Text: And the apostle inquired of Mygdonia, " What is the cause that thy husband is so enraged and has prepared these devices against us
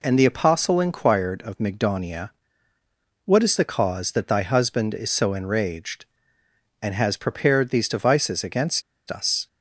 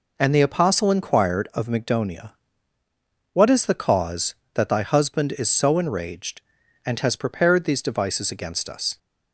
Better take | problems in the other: second | pauses between "against" and "us"; slight; at 8.8 s; 0.28 s long

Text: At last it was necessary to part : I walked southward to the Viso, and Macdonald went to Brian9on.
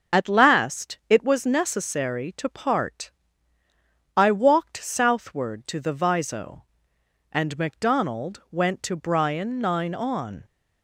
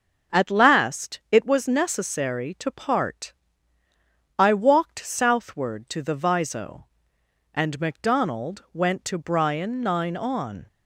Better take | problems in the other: second | loses the start of "At"; at 0.1 s; 30 ms // starts louder than the rest; until 1.2 s; 6.5 dB; also in the second

